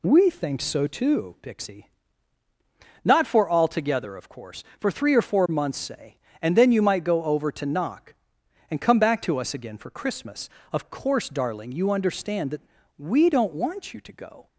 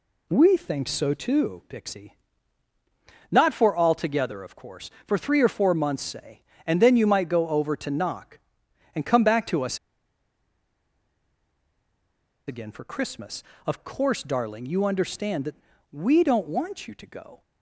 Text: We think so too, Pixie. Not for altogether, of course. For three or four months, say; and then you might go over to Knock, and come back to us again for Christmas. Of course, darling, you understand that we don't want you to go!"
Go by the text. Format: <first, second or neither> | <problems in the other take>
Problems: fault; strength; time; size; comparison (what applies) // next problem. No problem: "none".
first | pauses between "us" and "again"; strong; at 9.7 s; 2.7 s long // pauses between "that" and "we"; slight; at 15.5 s; 0.36 s long; slight in the first